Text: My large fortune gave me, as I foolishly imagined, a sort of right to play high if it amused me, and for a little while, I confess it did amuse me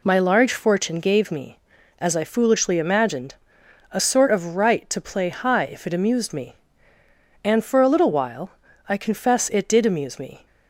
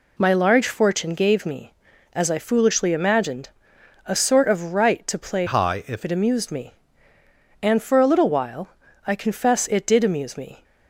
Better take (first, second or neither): first